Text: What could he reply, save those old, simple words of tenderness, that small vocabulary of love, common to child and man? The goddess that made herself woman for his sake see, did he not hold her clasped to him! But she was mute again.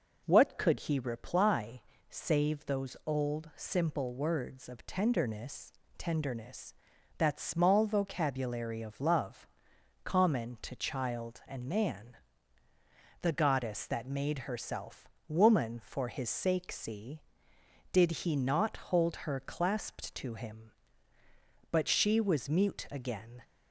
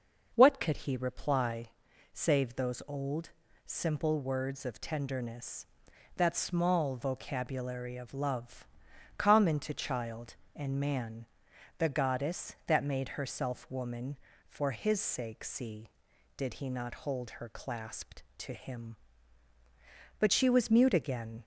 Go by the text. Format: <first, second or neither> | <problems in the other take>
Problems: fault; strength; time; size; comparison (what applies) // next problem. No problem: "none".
second | says "tenderness" twice; at 5.9 s // pauses between "herself" and "woman"; slight; at 15.0 s; 0.20 s long